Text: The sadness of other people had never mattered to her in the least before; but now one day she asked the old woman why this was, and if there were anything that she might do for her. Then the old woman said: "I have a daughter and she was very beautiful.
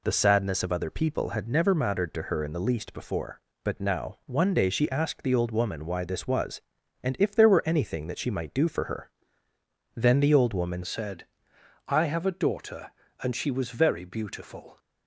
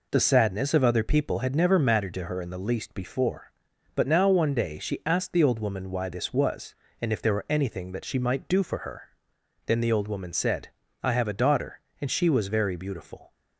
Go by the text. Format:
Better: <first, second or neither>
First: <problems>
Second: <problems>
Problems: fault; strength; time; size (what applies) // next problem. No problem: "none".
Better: second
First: changes voice at "said"; from 10.8 s on; 3.9 s long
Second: none